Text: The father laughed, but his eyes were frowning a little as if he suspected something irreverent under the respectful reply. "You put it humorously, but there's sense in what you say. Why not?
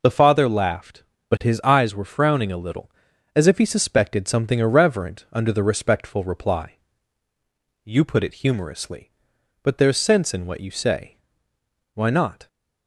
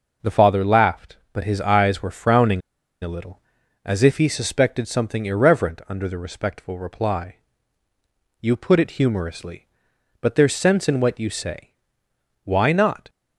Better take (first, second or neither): first